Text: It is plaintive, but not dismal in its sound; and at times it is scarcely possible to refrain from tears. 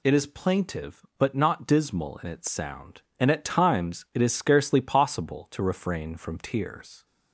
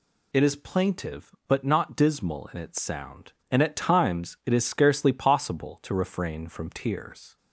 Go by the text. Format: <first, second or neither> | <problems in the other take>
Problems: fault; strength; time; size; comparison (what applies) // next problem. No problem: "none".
neither | none